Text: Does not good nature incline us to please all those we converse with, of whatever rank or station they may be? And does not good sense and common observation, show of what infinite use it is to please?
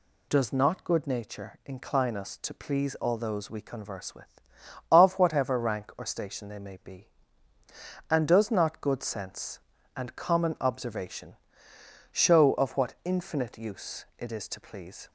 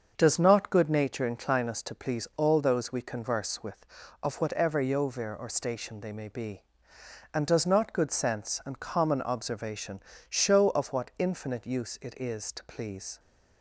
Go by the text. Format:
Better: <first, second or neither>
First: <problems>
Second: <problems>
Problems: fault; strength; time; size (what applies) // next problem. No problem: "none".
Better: first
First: none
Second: starts louder than the rest; until 1.1 s; 6.5 dB // says "yovir" for "rank"; at 4.8 s